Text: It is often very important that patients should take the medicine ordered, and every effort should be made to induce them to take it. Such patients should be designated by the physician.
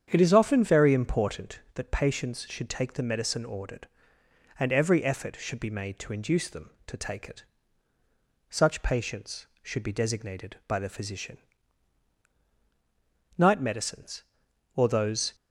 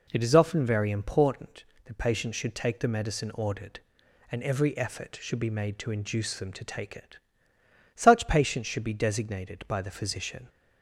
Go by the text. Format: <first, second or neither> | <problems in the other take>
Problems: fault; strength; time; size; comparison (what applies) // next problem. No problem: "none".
second | starts louder than the rest; strong; until 1.1 s; 8.5 dB // goes on to say "Night medicines or those"; strong; from 13.3 s on; 1.9 s long